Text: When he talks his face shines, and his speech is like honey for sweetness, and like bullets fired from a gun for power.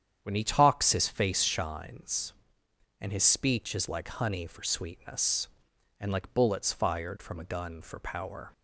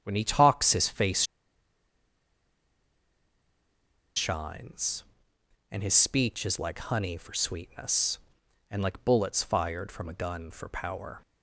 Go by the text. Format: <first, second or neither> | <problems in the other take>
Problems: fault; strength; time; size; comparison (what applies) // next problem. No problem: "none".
first | starts louder than the rest; strong; until 1.0 s; 8.5 dB; strong in the first // pauses between "face" and "shines"; strong; at 1.2 s; 2.9 s long